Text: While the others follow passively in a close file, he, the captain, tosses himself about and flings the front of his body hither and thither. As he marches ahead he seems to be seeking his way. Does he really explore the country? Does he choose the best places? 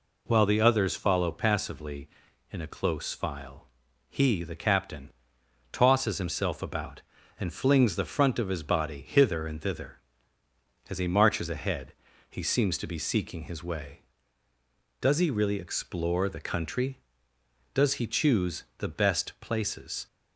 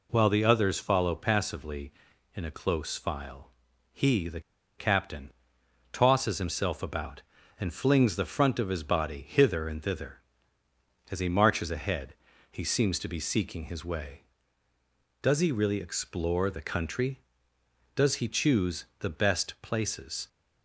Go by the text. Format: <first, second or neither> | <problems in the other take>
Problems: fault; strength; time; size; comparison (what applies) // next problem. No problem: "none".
first | pauses between "the" and "captain"; at 4.4 s; 0.37 s long // pauses between "ahead" and "he"; at 12.1 s; 0.38 s long; also in the first